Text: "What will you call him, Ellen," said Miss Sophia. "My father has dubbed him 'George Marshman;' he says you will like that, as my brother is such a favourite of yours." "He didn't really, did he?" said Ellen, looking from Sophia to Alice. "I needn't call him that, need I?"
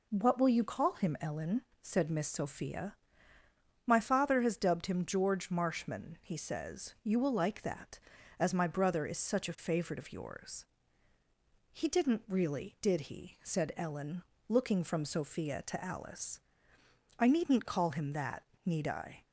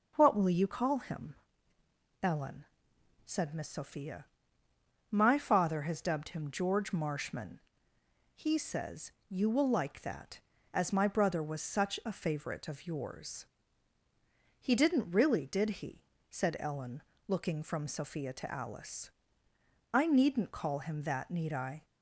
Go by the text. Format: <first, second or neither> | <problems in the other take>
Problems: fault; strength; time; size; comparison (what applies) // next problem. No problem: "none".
first | pauses between "says" and "you"; slight; at 9.1 s; 0.18 s long // says "was" for "is"; at 11.4 s